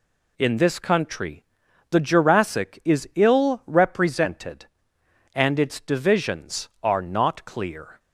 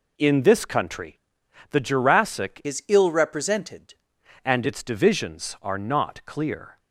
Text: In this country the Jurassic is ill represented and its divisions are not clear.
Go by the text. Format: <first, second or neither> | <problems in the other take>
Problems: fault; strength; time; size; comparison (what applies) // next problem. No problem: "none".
first | pauses between "country" and "the"; noticeable; at 1.1 s; 0.54 s long; noticeable in the first // changes voice from "is" to "represented"; from 2.6 to 3.9 s; 1.3 s long